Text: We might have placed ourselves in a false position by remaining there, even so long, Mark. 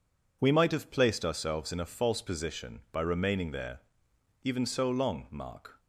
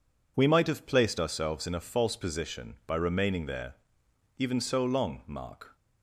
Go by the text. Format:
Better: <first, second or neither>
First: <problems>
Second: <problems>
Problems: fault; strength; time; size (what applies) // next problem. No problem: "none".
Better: neither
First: none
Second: none